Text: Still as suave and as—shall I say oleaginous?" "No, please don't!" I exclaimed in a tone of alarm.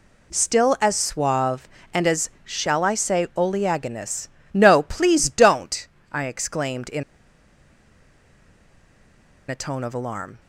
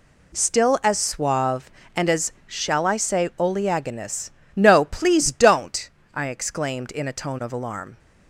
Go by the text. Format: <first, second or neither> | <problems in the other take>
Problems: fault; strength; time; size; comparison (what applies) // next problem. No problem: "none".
second | pauses between "in" and "a"; strong; at 7.0 s; 2.4 s long